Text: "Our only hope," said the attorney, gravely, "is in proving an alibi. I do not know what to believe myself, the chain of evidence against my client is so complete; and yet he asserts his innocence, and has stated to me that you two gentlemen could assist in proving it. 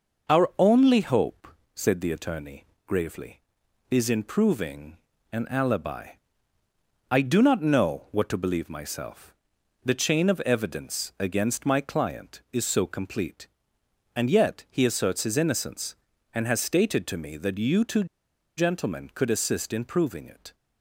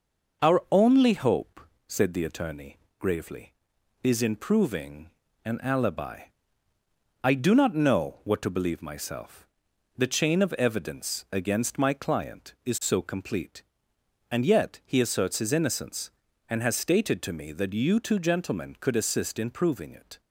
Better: second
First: pauses between "proving" and "an"; slight; at 4.9 s; 0.36 s long // pauses between "two" and "gentlemen"; noticeable; at 18.0 s; 0.52 s long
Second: pauses between "proving" and "an"; slight; at 5.0 s; 0.36 s long

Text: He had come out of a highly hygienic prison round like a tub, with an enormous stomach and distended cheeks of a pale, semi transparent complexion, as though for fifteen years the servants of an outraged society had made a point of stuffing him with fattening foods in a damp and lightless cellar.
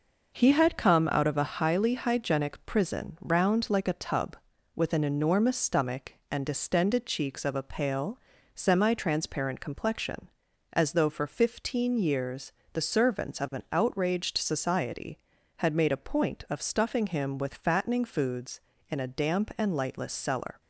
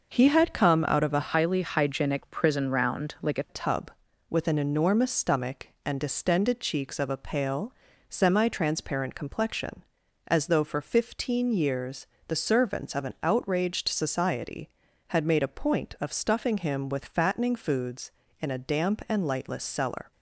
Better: first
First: pauses between "years" and "the"; slight; at 12.5 s; 0.22 s long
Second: changes voice from "highly" to "a"; from 1.3 to 3.4 s; 2.1 s long // pauses between "years" and "the"; slight; at 12.0 s; 0.22 s long

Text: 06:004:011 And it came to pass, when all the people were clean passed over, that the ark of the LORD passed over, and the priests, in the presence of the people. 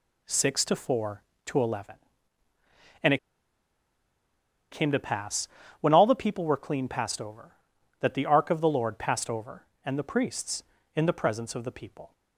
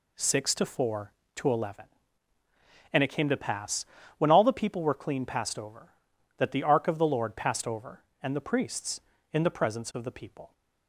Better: second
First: pauses between "it" and "came"; strong; at 3.1 s; 1.5 s long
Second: none

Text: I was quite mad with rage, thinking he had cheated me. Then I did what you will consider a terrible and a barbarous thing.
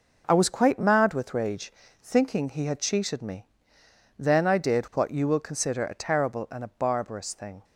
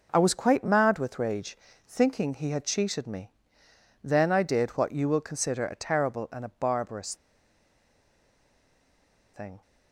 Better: first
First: none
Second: pauses between "barbarous" and "thing"; strong; at 7.1 s; 2.1 s long

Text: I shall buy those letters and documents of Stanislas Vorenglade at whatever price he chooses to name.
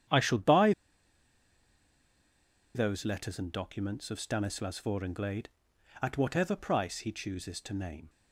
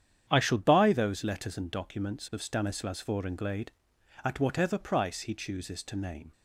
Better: second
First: starts louder than the rest; strong; until 3.1 s; 9 dB // pauses between "buy" and "those"; strong; at 0.7 s; 2.0 s long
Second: starts louder than the rest; strong; until 1.2 s; 9 dB

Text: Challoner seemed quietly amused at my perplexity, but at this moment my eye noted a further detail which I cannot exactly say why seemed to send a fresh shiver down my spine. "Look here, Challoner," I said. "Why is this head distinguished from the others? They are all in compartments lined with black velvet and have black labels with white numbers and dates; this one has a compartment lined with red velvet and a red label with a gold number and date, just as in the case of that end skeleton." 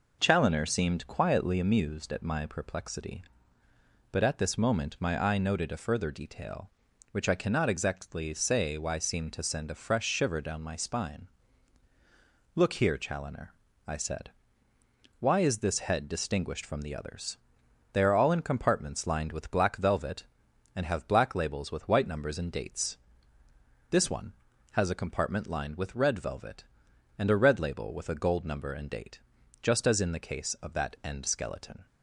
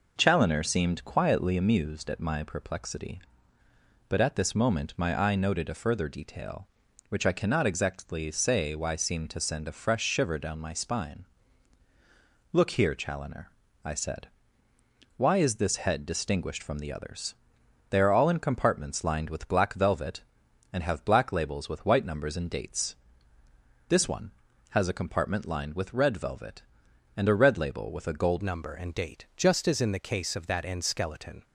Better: first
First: none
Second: changes voice at "number"; from 28.4 s on; 3.0 s long

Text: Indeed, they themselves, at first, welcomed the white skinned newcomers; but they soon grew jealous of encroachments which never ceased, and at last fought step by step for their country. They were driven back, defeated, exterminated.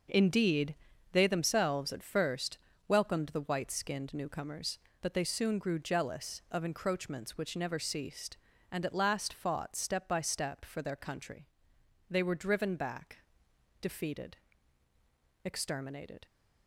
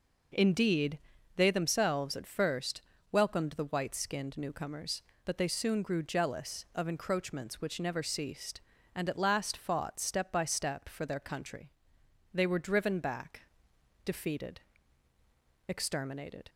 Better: second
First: gets quieter; strong; throughout; 9 dB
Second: none

